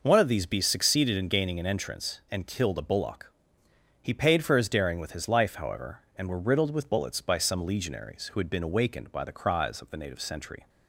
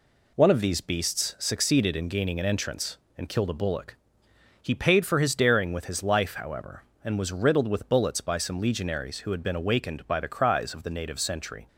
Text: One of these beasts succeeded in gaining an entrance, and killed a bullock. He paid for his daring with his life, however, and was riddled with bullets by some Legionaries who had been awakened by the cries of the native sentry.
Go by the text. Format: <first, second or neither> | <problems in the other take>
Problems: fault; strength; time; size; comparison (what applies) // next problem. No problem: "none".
second | says "were" for "was"; at 6.2 s